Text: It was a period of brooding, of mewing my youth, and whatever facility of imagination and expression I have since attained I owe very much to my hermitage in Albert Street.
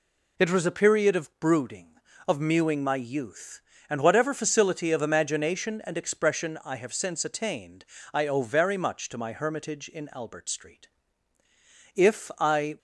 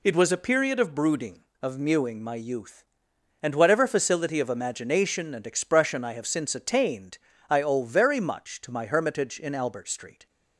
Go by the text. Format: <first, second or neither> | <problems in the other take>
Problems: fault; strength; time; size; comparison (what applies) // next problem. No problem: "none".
second | pauses between "attained" and "I"; slight; at 7.8 s; 0.26 s long; slight in the second // goes on to say "If I"; noticeable; from 11.9 s on; 0.82 s long